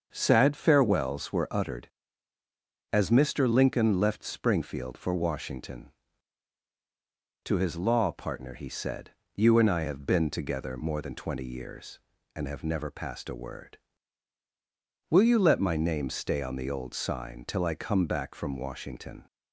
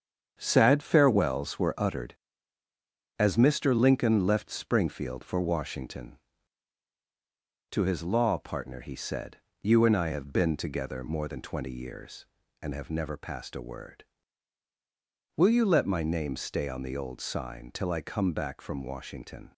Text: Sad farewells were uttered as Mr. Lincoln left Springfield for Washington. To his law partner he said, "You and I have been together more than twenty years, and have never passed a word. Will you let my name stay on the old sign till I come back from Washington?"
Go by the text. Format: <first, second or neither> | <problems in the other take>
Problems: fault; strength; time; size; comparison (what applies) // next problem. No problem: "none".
first | gets quieter; throughout; 6.5 dB // starts louder than the rest; strong; until 1.3 s; 7.5 dB; also in the first